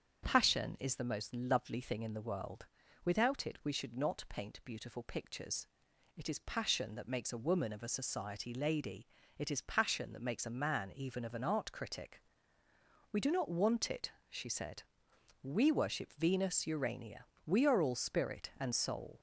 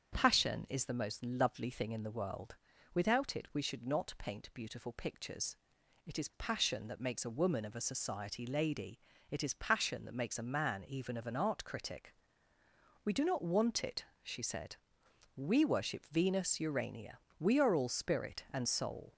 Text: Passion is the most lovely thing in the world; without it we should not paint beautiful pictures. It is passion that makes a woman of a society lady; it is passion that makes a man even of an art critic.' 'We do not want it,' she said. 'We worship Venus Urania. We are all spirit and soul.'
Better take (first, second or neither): neither